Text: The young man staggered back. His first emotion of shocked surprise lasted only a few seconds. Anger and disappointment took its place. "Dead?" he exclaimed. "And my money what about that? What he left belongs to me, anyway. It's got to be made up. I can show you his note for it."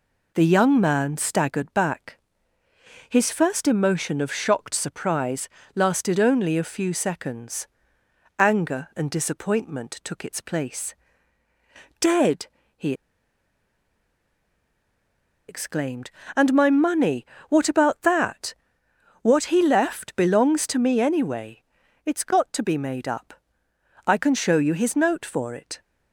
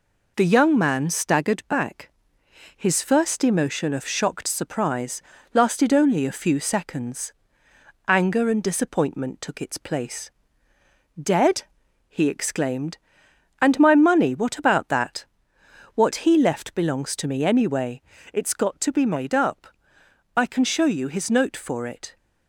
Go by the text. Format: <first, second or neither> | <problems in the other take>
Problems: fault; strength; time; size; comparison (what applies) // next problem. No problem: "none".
second | pauses between "surprise" and "lasted"; slight; at 5.4 s; 0.26 s long; slight in the second // pauses between "he" and "exclaimed"; strong; at 12.9 s; 2.5 s long // pauses between "money" and "what"; slight; at 17.2 s; 0.22 s long